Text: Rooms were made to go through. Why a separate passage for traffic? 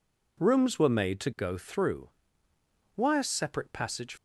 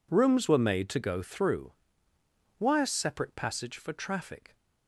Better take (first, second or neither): second